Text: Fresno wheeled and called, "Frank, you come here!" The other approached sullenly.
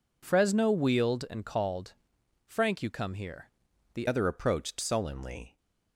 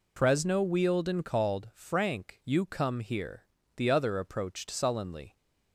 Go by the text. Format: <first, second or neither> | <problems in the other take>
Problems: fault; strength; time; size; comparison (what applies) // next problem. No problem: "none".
second | changes voice at "other"; from 4.0 s on; 1.5 s long